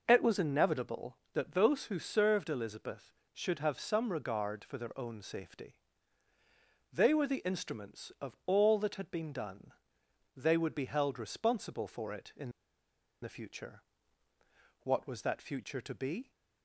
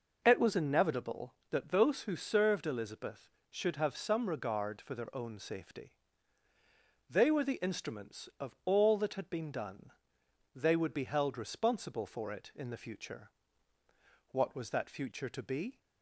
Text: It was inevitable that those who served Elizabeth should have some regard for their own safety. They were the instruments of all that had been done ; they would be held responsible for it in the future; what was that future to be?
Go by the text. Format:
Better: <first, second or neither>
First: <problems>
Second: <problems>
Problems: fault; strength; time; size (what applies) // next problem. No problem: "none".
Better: second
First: pauses between "in" and "the"; noticeable; at 12.5 s; 0.71 s long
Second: none